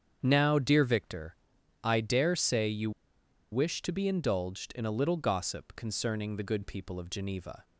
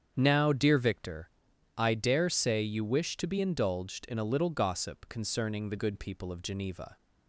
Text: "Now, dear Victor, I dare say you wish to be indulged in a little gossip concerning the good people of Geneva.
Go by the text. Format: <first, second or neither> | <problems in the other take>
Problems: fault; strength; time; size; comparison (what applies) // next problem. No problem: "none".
second | starts louder than the rest; strong; until 1.2 s; 8 dB; strong in the second // pauses between "you" and "wish"; noticeable; at 2.9 s; 0.61 s long